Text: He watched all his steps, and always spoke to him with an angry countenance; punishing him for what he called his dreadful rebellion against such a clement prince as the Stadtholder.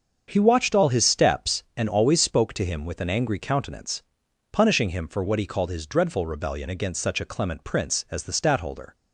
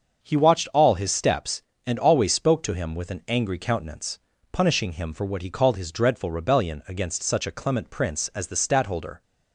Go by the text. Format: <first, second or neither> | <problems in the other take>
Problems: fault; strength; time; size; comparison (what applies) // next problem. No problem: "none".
neither | starts louder than the rest; the same in both